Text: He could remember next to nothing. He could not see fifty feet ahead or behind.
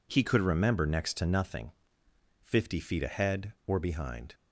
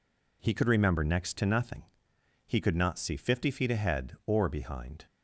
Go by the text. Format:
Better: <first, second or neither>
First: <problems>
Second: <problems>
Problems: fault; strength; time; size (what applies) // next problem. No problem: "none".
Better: second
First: skips "He could not see"; at 2.0 s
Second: none